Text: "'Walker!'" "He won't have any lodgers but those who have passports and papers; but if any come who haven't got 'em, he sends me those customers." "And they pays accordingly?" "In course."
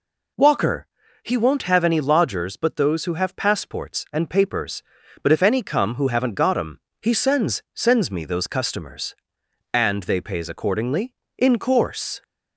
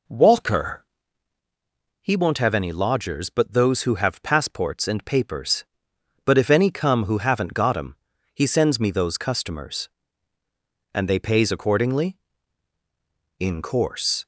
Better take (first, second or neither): second